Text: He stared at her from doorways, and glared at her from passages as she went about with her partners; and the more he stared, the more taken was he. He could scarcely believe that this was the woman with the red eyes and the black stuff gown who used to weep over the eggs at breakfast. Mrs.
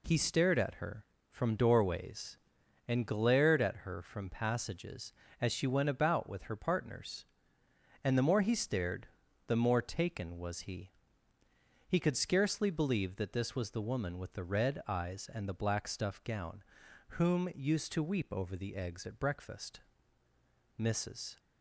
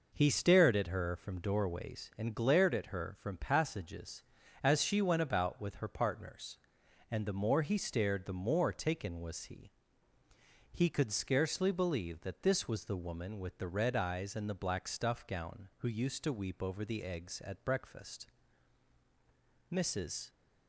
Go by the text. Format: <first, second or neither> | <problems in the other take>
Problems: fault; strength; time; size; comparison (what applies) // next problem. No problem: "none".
second | says "whom" for "who"; at 17.1 s